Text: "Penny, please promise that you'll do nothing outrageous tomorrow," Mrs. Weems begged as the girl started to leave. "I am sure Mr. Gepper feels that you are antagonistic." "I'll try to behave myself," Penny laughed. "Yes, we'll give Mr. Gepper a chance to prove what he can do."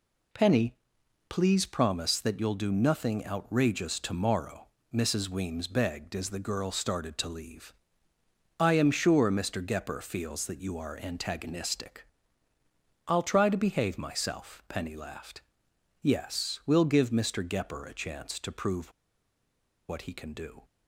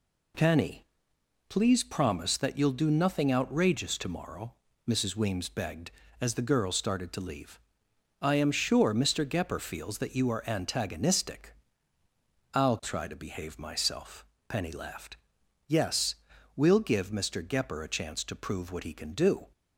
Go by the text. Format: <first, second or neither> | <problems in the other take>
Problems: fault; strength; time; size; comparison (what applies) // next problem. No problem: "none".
second | pauses between "prove" and "what"; noticeable; at 18.9 s; 0.97 s long